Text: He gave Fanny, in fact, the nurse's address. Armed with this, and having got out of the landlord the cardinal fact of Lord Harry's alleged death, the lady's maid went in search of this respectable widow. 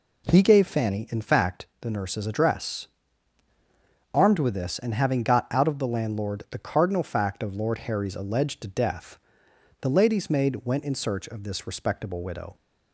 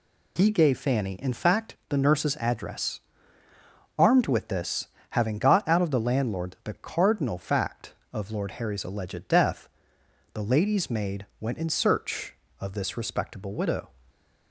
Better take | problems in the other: first | skips "and"; at 4.9 s // pauses between "maid" and "went"; slight; at 11.2 s; 0.16 s long

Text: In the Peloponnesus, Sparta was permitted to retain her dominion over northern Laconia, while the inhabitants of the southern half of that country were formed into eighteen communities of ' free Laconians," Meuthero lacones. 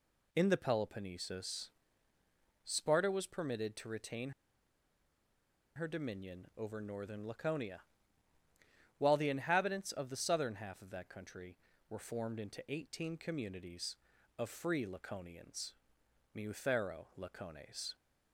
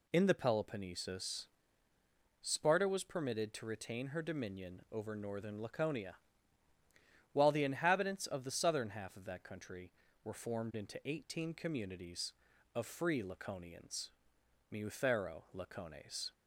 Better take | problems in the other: second | pauses between "retain" and "her"; strong; at 4.3 s; 1.4 s long

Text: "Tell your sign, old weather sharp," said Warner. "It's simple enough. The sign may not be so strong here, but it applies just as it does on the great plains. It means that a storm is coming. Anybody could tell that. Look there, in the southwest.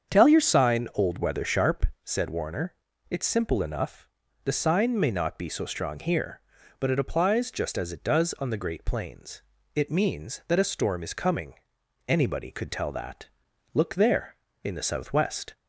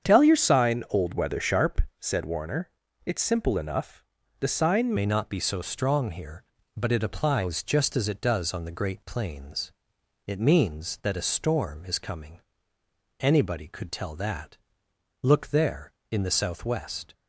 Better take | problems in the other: first | starts louder than the rest; strong; until 1.1 s; 8 dB; strong in the first // changes voice at "may"; from 4.9 s on; 12.2 s long

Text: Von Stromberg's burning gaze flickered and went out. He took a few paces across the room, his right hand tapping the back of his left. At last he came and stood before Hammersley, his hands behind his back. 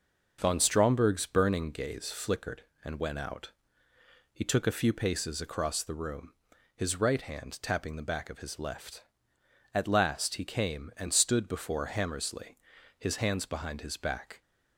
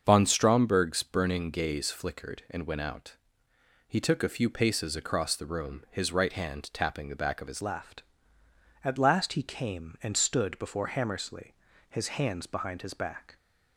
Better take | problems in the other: first | starts louder than the rest; until 1.0 s; 7 dB // changes voice at "left"; from 7.6 s on; 5.7 s long

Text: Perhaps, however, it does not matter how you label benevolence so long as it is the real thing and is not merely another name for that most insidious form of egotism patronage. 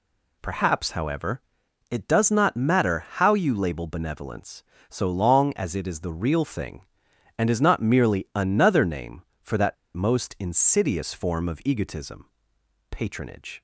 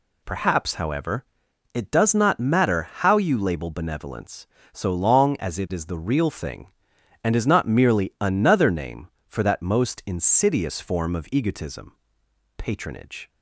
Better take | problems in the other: second | pauses between "that" and "most"; slight; at 9.7 s; 0.20 s long // pauses between "egotism" and "patronage"; noticeable; at 12.2 s; 0.64 s long; noticeable in the second

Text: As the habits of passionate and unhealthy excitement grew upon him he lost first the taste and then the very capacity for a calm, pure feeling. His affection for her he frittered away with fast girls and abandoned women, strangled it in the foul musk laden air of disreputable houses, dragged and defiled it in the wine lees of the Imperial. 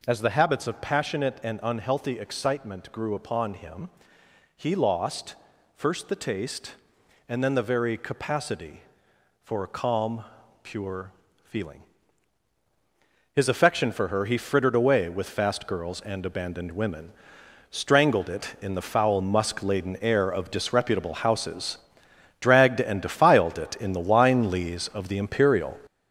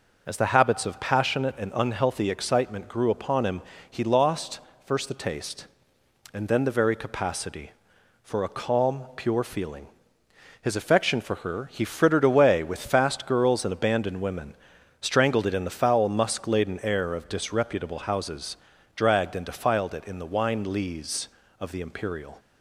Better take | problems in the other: second | gets louder; noticeable; throughout; 6 dB // pauses between "him" and "he"; noticeable; at 3.8 s; 0.68 s long; slight in the second // pauses between "lost" and "first"; at 5.3 s; 0.40 s long; slight in the second // pauses between "pure" and "feeling"; at 11.1 s; 0.38 s long

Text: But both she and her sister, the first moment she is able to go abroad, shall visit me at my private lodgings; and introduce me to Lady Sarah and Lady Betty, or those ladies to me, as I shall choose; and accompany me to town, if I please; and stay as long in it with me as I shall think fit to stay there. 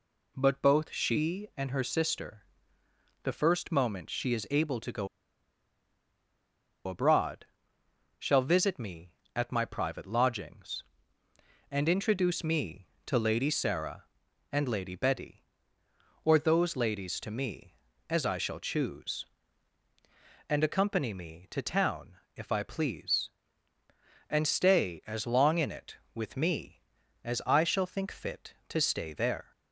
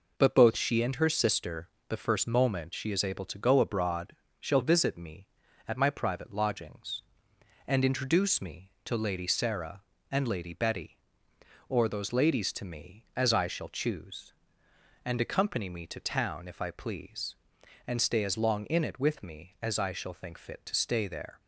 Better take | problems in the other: second | pauses between "go" and "abroad"; strong; at 5.0 s; 1.7 s long

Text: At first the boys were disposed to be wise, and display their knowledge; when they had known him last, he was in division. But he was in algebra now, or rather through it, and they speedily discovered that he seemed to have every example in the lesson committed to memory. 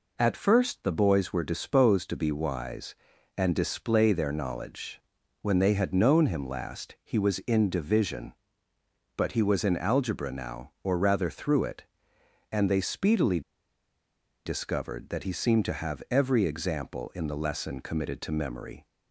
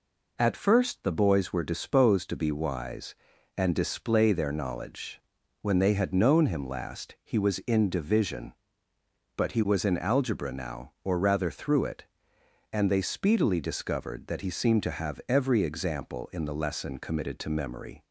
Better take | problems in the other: second | pauses between "speedily" and "discovered"; at 13.4 s; 1.0 s long

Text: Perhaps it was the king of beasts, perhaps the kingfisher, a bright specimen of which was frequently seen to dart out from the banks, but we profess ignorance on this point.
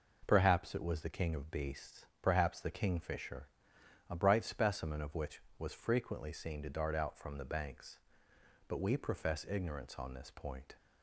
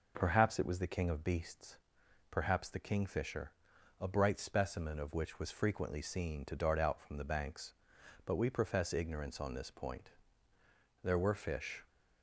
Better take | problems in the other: first | goes on to say "There were fish"; noticeable; from 11.0 s on; 0.82 s long

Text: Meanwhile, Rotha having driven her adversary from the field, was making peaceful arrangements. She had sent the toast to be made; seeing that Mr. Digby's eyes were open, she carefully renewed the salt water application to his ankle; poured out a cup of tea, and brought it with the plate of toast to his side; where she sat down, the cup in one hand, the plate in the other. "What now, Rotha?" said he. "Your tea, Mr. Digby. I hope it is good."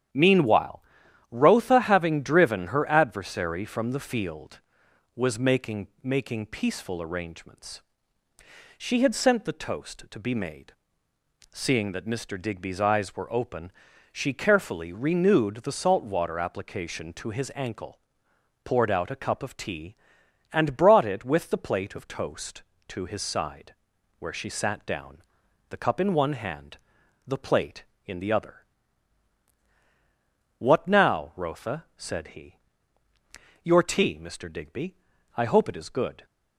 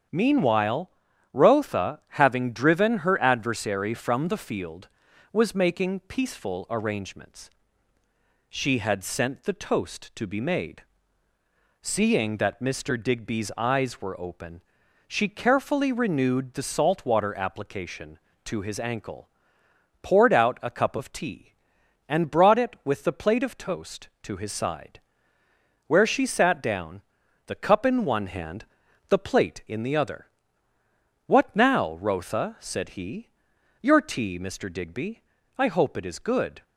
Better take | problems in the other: second | starts louder than the rest; strong; until 1.6 s; 10 dB; strong in the second // says "making" twice; at 6.0 s

